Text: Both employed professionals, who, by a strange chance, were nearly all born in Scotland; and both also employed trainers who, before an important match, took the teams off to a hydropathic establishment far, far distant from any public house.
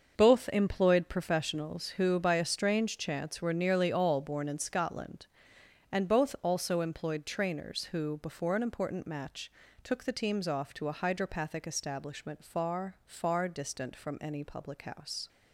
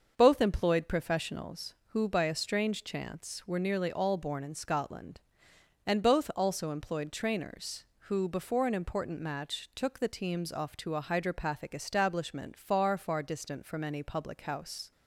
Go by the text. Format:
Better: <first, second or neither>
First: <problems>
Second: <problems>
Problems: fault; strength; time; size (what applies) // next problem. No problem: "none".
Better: neither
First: starts louder than the rest; until 1.1 s; 6.5 dB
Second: starts louder than the rest; until 1.1 s; 6.5 dB